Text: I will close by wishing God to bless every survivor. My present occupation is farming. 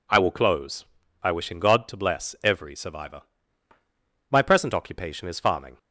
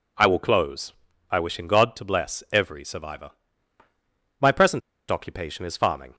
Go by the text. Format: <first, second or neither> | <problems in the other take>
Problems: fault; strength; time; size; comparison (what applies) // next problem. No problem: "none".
first | pauses between "present" and "occupation"; slight; at 4.8 s; 0.30 s long